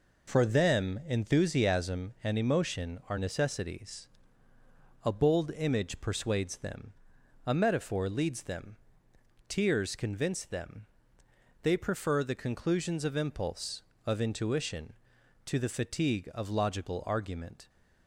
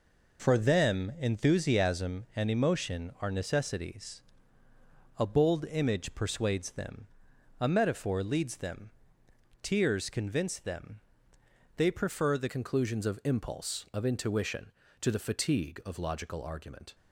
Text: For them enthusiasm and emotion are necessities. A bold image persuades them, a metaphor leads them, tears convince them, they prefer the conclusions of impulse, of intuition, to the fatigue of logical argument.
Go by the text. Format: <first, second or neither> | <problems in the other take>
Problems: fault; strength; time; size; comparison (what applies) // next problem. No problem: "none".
first | changes voice at "conclusions"; from 12.4 s on; 4.5 s long